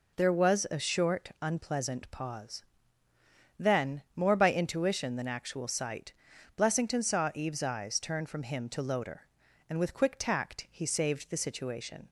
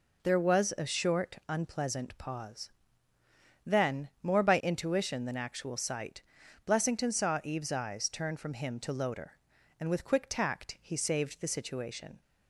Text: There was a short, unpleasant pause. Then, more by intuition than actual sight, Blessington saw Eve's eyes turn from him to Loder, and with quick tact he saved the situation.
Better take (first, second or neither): neither